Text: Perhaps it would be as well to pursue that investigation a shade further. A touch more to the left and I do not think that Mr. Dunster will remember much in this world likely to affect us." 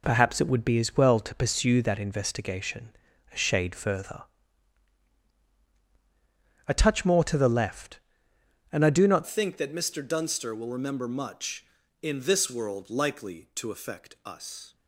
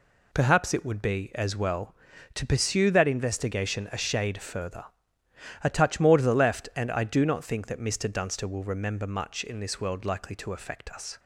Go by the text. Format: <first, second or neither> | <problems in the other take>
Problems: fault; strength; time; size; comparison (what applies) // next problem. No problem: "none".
second | pauses between "investigation" and "a"; at 2.9 s; 0.42 s long // changes voice at "think"; from 9.2 s on; 5.5 s long